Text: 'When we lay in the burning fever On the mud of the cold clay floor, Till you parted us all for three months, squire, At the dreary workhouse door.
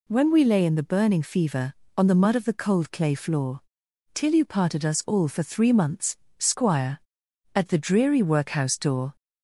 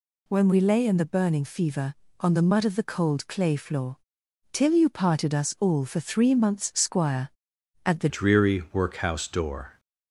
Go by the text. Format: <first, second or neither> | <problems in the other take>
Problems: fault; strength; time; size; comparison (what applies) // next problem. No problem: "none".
first | changes voice at "dreary"; from 8.0 s on; 1.7 s long